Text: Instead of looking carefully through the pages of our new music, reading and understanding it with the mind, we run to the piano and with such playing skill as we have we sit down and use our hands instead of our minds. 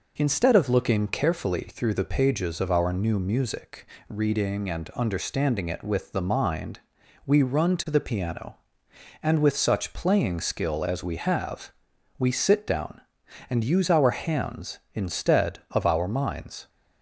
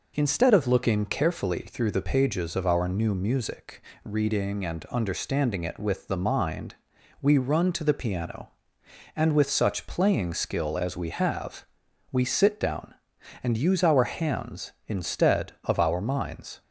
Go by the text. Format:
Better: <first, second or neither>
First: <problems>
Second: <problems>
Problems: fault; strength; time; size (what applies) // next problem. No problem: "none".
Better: neither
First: pauses between "have" and "we"; noticeable; at 11.7 s; 0.46 s long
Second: pauses between "have" and "we"; noticeable; at 11.6 s; 0.46 s long